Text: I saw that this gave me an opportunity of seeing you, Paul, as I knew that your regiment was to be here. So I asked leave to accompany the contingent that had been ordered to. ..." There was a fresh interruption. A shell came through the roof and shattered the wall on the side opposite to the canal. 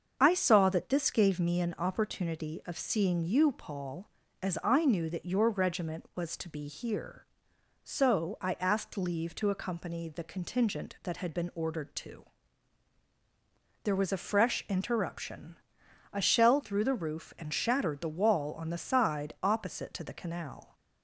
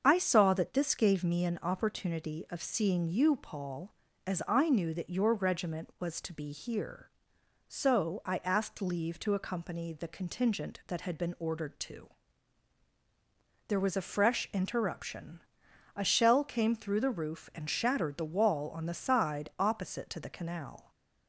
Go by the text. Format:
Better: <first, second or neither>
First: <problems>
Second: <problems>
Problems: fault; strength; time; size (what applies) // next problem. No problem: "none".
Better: second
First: starts louder than the rest; until 1.2 s; 7 dB // skips "came"; at 16.6 s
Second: starts louder than the rest; until 1.0 s; 7 dB